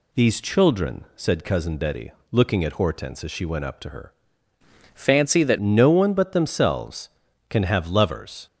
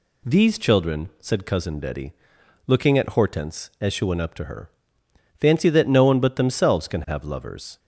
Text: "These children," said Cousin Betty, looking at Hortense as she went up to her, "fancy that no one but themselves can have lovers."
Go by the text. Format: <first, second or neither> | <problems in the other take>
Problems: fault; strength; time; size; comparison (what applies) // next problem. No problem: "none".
second | changes voice from "fancy" to "that"; from 4.9 to 5.5 s; 0.6 s long